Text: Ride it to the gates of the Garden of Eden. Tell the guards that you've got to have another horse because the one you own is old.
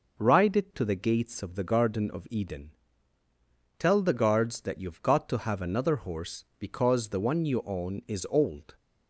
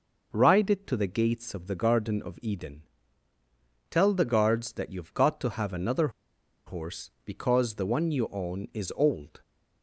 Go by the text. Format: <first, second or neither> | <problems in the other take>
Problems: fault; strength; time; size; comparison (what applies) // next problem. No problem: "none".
first | pauses between "another" and "horse"; noticeable; at 6.0 s; 0.57 s long